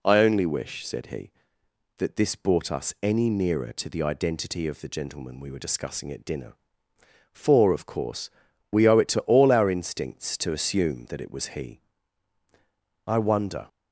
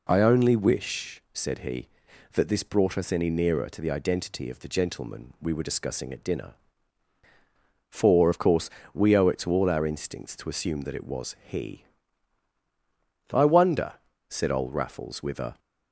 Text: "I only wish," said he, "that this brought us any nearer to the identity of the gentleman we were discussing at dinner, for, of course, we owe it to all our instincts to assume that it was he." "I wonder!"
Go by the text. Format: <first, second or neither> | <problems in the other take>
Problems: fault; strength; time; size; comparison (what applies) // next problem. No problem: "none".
first | goes on to say "said old Raffles with a"; noticeable; from 14.2 s on; 1.3 s long